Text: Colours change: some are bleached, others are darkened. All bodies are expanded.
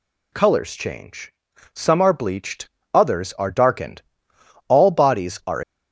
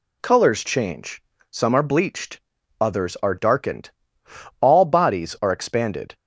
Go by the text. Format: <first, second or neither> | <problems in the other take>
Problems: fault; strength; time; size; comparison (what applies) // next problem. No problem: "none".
second | stops before "expanded"; at 5.6 s